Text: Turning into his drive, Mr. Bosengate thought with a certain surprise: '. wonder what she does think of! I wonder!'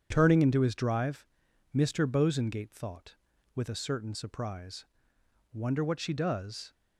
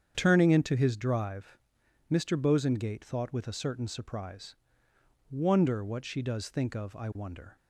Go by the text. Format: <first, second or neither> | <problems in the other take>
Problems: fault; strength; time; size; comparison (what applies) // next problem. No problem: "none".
second | starts louder than the rest; strong; until 1.1 s; 8.5 dB; strong in the second // stops before "think of I wonder"; at 6.7 s